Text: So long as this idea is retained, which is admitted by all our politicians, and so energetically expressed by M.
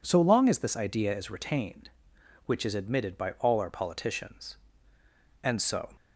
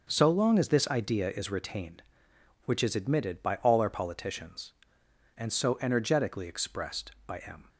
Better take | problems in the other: second | stops before "energetically expressed by M"; at 5.9 s

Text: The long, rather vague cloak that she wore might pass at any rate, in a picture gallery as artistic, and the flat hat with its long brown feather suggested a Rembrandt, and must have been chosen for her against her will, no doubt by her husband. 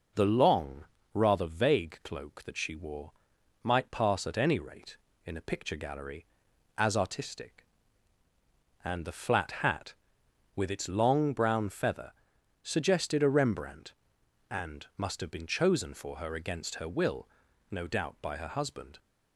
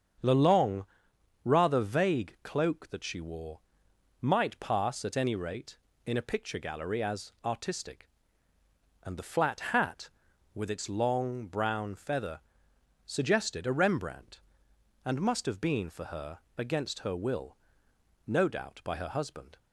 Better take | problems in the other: first | starts louder than the rest; strong; until 1.8 s; 7.5 dB // pauses between "wore" and "might"; noticeable; at 3.6 s; 0.59 s long; noticeable in the first // pauses between "feather" and "suggested"; noticeable; at 12.4 s; 0.66 s long; noticeable in the first // skips "chosen"; at 15.8 s // pauses between "her" and "against"; slight; at 16.3 s; 0.18 s long

